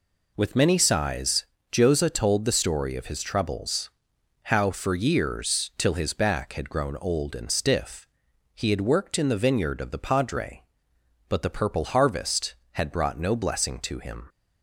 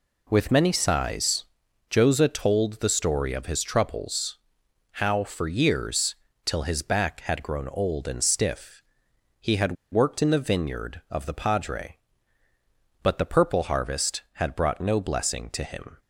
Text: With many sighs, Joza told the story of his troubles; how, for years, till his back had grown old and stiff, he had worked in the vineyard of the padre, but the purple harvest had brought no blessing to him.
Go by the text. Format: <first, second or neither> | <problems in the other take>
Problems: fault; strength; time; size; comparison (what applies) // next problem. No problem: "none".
first | pauses between "had" and "worked"; slight; at 9.7 s; 0.17 s long